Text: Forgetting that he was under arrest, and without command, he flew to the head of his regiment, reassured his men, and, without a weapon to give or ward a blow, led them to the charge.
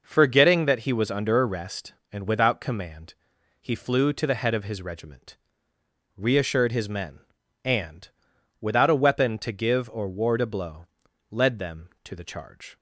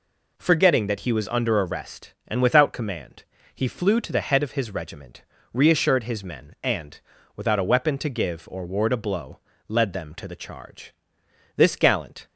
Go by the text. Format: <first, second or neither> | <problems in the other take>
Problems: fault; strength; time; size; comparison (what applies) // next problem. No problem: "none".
first | goes on to say "This gallant"; noticeable; from 11.5 s on; 0.70 s long